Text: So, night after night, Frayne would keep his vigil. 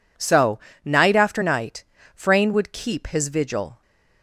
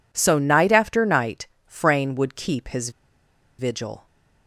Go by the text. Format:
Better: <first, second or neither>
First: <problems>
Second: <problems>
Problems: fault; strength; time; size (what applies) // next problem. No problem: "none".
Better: first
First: none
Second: pauses between "his" and "vigil"; noticeable; at 2.8 s; 0.68 s long